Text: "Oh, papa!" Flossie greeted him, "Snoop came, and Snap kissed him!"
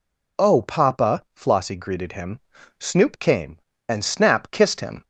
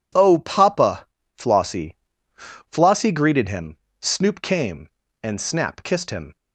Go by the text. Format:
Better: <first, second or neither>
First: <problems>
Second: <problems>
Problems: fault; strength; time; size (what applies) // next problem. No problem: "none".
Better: first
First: none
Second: says "Flossie" twice; at 2.3 s